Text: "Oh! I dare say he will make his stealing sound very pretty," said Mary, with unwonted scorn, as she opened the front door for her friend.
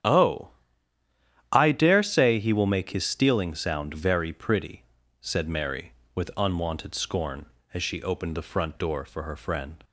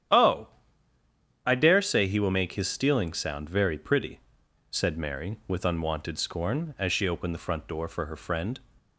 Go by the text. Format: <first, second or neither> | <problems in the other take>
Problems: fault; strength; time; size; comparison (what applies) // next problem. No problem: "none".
neither | starts louder than the rest; strong; the same in both